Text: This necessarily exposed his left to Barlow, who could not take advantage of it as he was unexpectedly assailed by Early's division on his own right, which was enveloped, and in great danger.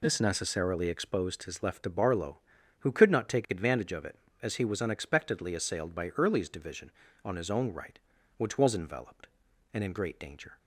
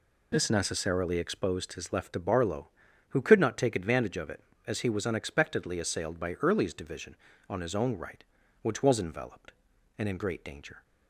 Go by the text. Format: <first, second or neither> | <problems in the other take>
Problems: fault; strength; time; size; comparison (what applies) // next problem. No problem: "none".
neither | none